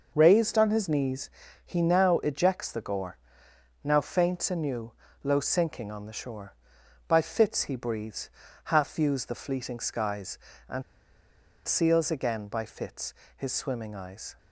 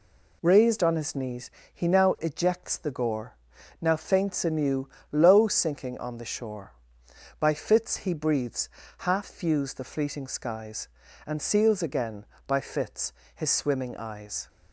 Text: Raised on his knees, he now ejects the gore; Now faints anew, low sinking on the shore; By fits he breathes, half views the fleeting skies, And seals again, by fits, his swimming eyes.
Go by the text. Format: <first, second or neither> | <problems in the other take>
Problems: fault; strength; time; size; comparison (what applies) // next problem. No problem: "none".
second | pauses between "And" and "seals"; noticeable; at 10.8 s; 0.84 s long